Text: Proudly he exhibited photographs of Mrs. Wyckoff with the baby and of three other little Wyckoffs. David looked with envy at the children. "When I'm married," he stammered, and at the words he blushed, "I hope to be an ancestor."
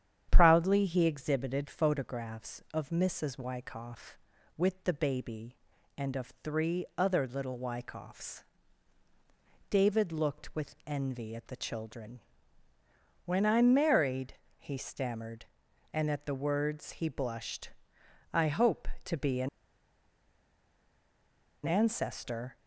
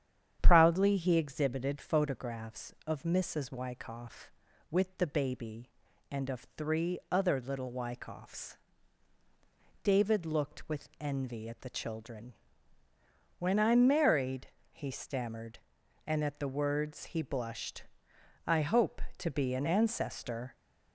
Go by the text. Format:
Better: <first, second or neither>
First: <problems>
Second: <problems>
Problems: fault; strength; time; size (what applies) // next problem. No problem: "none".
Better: second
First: starts louder than the rest; strong; until 1.3 s; 9 dB // pauses between "an" and "ancestor"; strong; at 19.4 s; 2.1 s long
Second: starts louder than the rest; strong; until 1.4 s; 9 dB